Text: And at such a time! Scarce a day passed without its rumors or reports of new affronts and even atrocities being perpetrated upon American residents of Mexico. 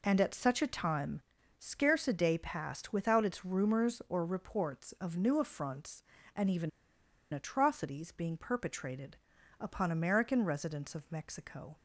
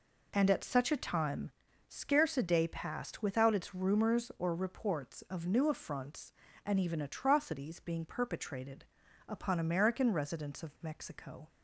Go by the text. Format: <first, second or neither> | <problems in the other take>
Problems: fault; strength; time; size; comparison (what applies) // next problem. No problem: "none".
second | pauses between "even" and "atrocities"; noticeable; at 6.6 s; 0.62 s long // pauses between "perpetrated" and "upon"; at 9.1 s; 0.42 s long; also in the second